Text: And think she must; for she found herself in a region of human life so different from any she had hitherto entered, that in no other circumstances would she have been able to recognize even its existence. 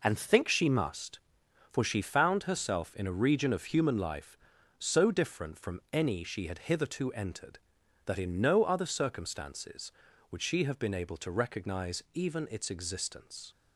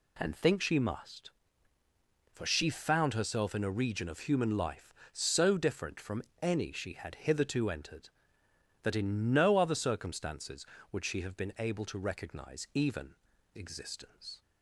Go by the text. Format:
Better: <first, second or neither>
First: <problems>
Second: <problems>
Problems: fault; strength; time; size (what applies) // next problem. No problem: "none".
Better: first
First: none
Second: pauses between "from" and "any"; slight; at 6.2 s; 0.18 s long // skips "its"; at 13.3 s